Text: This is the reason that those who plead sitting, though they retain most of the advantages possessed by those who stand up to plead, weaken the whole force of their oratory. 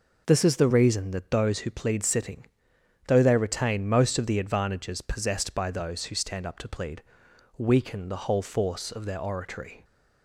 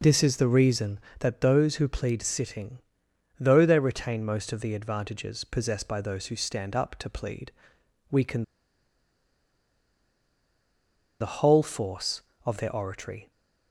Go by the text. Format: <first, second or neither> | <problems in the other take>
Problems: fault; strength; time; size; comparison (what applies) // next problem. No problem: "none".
first | pauses between "weaken" and "the"; strong; at 8.4 s; 2.7 s long